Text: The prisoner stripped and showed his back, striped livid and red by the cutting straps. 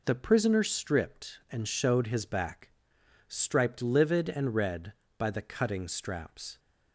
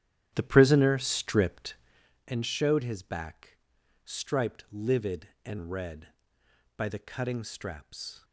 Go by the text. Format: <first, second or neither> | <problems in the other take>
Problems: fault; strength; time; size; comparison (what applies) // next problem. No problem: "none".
first | starts louder than the rest; strong; until 2.3 s; 10.5 dB